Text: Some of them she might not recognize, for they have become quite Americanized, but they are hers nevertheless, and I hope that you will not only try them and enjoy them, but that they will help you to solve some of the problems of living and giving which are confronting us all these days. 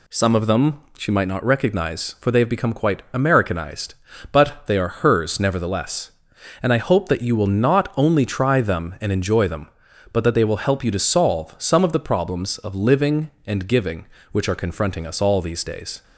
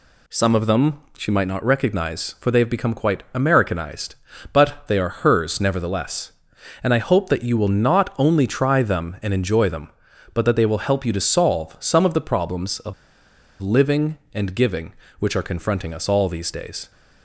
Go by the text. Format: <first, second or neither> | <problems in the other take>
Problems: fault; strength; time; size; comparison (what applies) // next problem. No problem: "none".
first | pauses between "them" and "she"; slight; at 1.0 s; 0.16 s long; slight in the first // pauses between "of" and "living"; noticeable; at 12.9 s; 0.68 s long